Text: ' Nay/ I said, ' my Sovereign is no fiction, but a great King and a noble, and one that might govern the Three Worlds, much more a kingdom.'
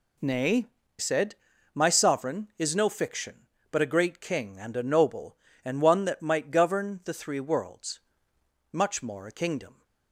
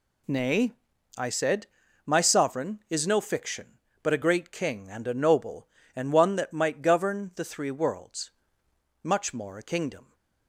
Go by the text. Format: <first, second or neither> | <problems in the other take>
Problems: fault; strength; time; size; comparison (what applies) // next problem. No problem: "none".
second | skips "I"; at 0.8 s